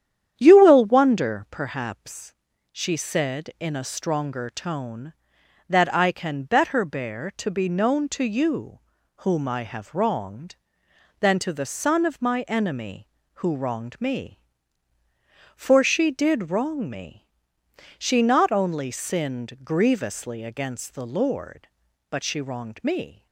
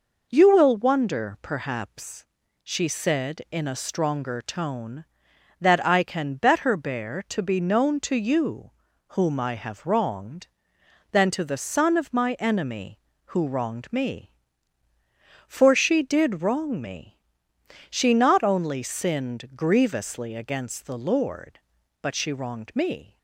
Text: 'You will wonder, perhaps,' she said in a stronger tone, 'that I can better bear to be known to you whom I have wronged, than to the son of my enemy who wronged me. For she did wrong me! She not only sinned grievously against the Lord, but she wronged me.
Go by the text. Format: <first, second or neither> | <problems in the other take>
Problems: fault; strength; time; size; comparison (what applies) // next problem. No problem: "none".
second | starts louder than the rest; strong; until 1.5 s; 9.5 dB // pauses between "you" and "whom"; at 8.7 s; 0.42 s long; also in the second